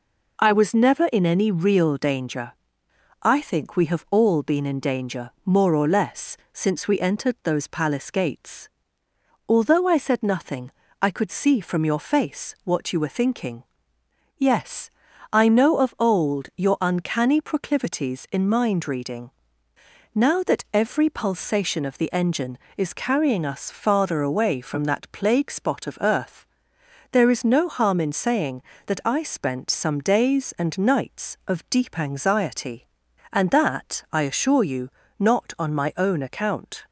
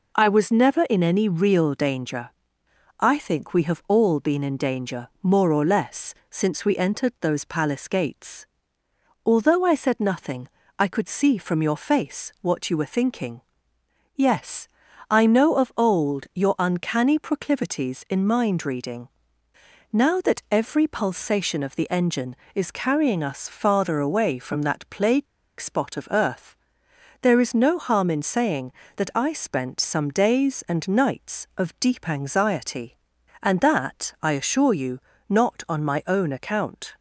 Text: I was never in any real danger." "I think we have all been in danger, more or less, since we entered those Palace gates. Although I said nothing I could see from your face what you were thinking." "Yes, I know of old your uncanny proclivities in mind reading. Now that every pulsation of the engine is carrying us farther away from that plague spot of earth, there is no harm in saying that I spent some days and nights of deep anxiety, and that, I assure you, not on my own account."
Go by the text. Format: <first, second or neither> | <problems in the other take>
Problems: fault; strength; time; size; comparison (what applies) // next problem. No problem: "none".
first | pauses between "nothing" and "I"; slight; at 10.4 s; 0.28 s long; slight in the first // pauses between "plague" and "spot"; slight; at 25.2 s; 0.33 s long